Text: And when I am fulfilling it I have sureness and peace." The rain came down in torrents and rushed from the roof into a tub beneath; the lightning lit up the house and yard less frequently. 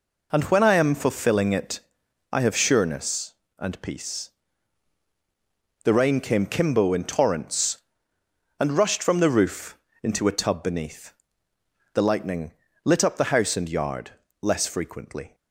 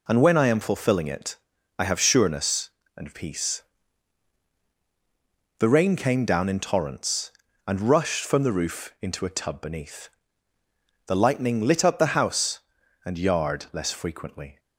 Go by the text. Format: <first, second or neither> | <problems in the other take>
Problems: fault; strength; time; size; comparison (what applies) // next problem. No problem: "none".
second | pauses between "it" and "I"; noticeable; at 1.8 s; 0.50 s long; also in the second // says "kimbo" for "down"; at 6.4 s // pauses between "roof" and "into"; slight; at 9.7 s; 0.26 s long // pauses between "lightning" and "lit"; slight; at 12.5 s; 0.32 s long // pauses between "yard" and "less"; slight; at 14.1 s; 0.30 s long